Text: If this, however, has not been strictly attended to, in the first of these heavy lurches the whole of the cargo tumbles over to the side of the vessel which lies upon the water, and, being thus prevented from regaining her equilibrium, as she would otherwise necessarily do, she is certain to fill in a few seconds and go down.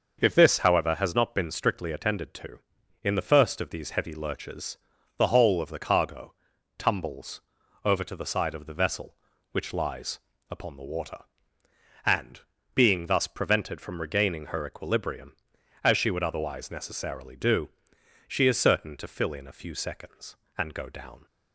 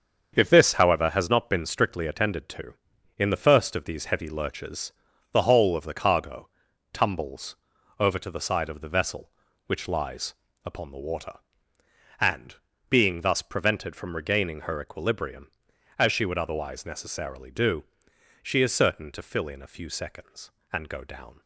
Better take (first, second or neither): first